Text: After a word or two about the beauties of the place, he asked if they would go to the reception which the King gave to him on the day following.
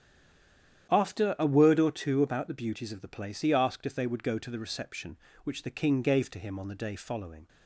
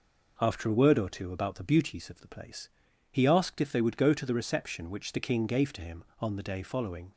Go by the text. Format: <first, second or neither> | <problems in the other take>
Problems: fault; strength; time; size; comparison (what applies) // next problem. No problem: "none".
second | stays silent before the first word; slight; until 0.8 s; 0.8 s long // starts louder than the rest; strong; until 1.9 s; 10 dB